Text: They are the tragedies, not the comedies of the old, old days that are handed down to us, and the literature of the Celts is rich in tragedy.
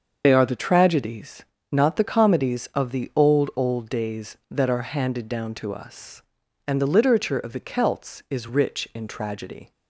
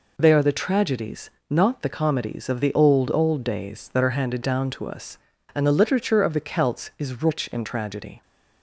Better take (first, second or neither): second